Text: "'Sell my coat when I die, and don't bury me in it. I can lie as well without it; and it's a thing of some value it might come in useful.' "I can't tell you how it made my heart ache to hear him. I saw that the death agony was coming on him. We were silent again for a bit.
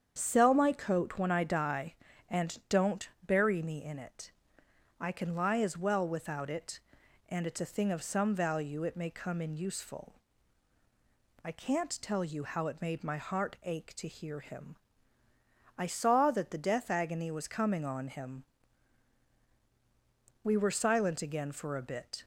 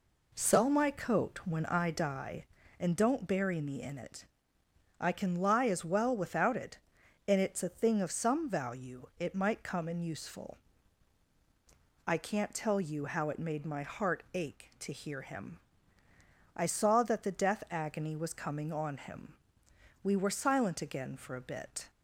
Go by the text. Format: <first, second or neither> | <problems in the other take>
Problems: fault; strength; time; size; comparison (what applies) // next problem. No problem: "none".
second | starts louder than the rest; strong; until 1.1 s; 8 dB // pauses between "don't" and "bury"; slight; at 3.0 s; 0.19 s long // says "may" for "might"; at 8.9 s